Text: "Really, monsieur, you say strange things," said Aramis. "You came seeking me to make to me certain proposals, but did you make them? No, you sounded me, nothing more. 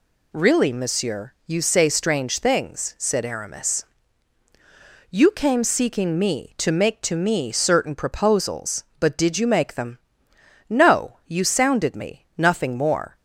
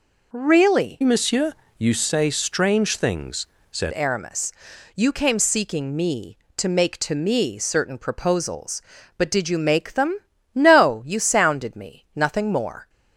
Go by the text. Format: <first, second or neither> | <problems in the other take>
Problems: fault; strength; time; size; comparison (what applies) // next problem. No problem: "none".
first | changes voice from "monsieur" to "said"; from 1.0 to 3.9 s; 2.9 s long